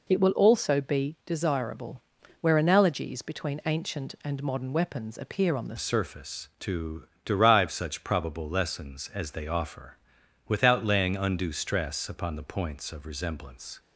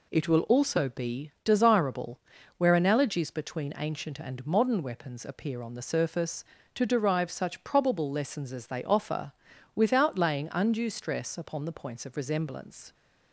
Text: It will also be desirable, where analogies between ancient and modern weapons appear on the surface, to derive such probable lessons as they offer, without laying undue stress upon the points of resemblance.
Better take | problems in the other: second | changes voice at "surface"; from 5.7 s on; 8.0 s long // pauses between "to" and "derive"; slight; at 7.0 s; 0.18 s long

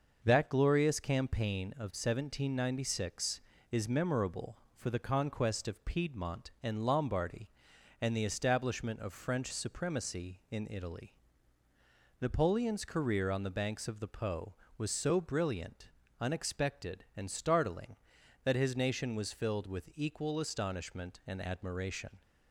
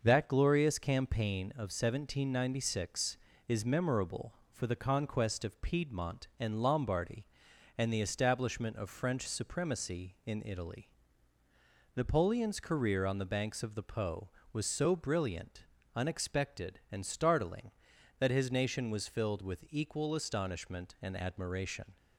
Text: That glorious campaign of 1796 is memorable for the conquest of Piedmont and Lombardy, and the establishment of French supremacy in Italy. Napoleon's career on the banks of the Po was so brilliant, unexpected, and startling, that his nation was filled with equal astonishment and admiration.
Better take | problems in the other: neither | starts louder than the rest; noticeable; the same in both

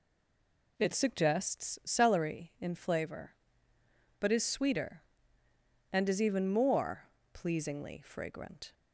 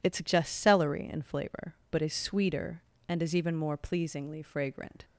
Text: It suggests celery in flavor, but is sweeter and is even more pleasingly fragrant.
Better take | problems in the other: second | stays silent before the first word; slight; until 0.7 s; 0.7 s long // pauses between "more" and "pleasingly"; slight; at 7.0 s; 0.26 s long

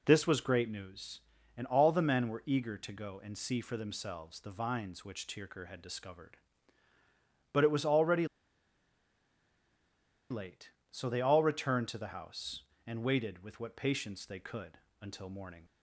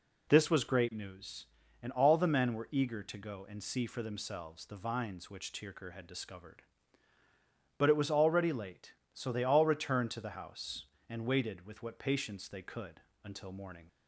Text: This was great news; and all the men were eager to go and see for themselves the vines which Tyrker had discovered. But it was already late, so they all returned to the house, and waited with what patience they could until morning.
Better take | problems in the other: second | pauses between "already" and "late"; strong; at 8.2 s; 2.0 s long // pauses between "could" and "until"; slight; at 14.7 s; 0.24 s long; slight in the second

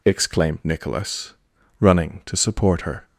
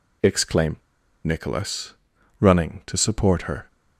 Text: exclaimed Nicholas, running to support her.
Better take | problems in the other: first | pauses between "exclaimed" and "Nicholas"; noticeable; at 0.7 s; 0.47 s long

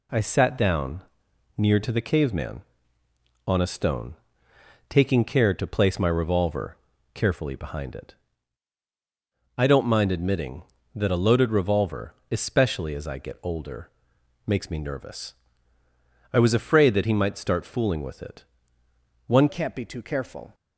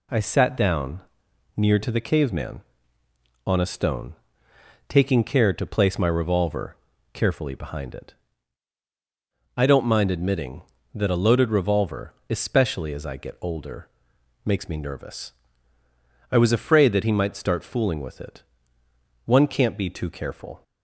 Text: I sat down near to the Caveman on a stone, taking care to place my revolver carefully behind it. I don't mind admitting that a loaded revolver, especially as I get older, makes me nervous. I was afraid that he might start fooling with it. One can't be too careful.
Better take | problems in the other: second | pauses between "down" and "near"; noticeable; at 1.0 s; 0.54 s long; noticeable in the second // pauses between "revolver" and "carefully"; at 6.7 s; 0.38 s long; also in the second // changes voice at "can't"; from 19.4 s on; 1.1 s long

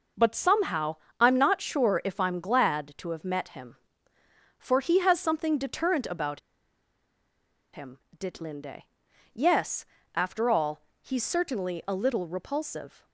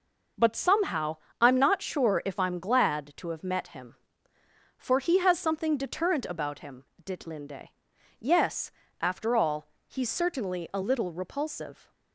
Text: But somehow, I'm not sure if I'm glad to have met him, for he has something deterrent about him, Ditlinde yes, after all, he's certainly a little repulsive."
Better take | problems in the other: second | pauses between "about" and "him"; strong; at 6.3 s; 1.3 s long // pauses between "Ditlinde" and "yes"; noticeable; at 8.8 s; 0.56 s long; noticeable in the second

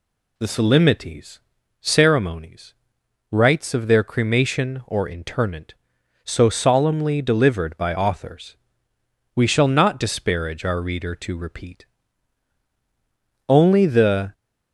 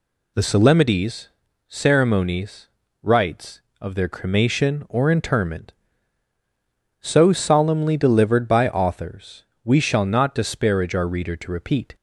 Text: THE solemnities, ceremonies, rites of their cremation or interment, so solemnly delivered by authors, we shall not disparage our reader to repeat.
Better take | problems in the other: second | goes on to say "Only the"; noticeable; from 13.4 s on; 0.86 s long

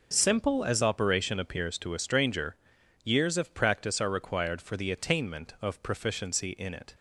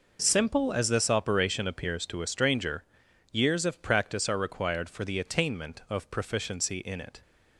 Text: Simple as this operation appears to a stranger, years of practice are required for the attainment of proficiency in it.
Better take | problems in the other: second | skips "this"; at 0.8 s

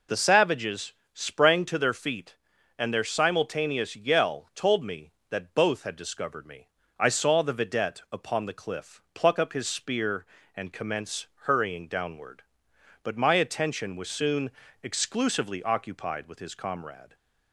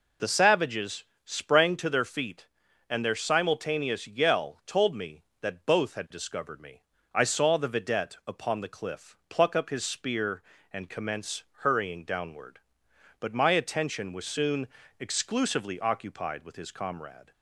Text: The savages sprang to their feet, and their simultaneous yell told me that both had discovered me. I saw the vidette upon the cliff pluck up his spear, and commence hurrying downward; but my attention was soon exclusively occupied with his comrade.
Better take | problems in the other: neither | pauses between "savages" and "sprang"; slight; the same in both // pauses between "commence" and "hurrying"; slight; the same in both // pauses between "soon" and "exclusively"; slight; the same in both

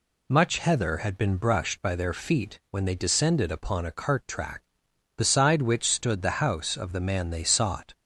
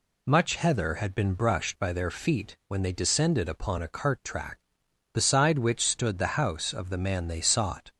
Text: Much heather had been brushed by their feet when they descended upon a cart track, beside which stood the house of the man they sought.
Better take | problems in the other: neither | none

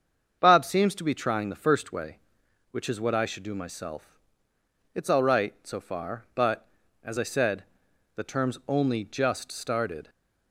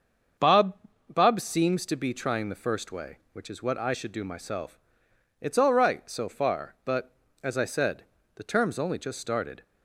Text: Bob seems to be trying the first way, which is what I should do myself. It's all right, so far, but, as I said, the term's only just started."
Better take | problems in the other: first | starts louder than the rest; until 1.7 s; 7 dB; also in the first // says "Bob" twice; at 1.1 s

